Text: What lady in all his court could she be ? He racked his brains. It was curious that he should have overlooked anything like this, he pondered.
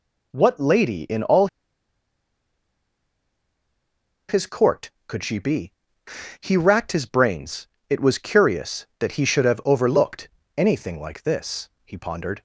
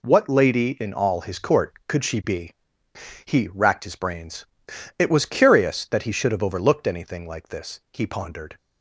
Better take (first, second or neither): second